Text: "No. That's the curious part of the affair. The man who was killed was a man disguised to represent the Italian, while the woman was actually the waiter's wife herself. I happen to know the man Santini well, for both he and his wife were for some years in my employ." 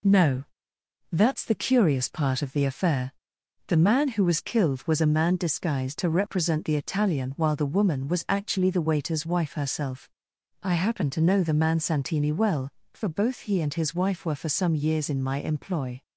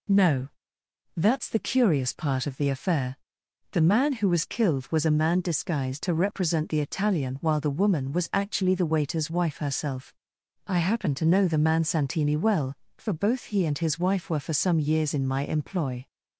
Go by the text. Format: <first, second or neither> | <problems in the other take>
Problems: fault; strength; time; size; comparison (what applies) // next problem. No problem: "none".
second | gets quieter; slight; throughout; 2.5 dB